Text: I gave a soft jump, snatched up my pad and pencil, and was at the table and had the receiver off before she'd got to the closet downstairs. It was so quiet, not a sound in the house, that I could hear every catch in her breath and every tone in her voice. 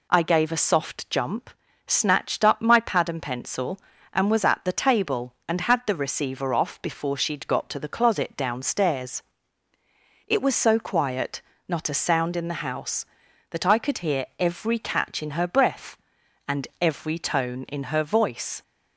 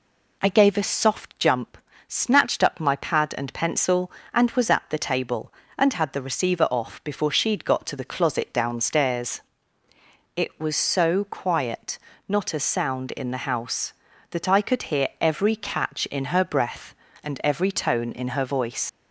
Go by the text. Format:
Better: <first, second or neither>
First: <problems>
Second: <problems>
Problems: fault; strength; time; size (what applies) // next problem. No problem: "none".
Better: first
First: none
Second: leaves "voice" unfinished; at 18.8 s; 110 ms